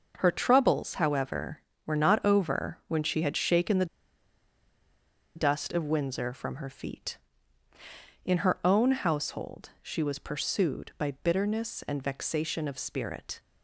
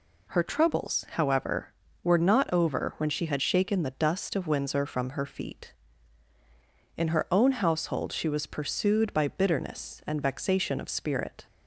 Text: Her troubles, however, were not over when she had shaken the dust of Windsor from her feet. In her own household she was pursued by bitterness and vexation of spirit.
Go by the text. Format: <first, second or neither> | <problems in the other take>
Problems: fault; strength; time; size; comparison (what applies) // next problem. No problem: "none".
second | pauses between "the" and "dust"; strong; at 3.8 s; 1.4 s long